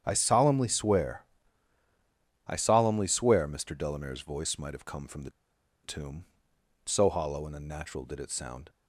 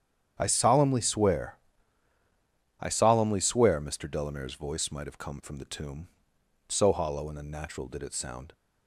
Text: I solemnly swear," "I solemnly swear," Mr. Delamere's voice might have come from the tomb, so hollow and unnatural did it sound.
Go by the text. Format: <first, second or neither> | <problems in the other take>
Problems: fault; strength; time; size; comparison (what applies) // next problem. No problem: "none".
second | starts louder than the rest; strong; until 1.0 s; 9 dB; strong in the second // pauses between "the" and "tomb"; noticeable; at 5.2 s; 0.53 s long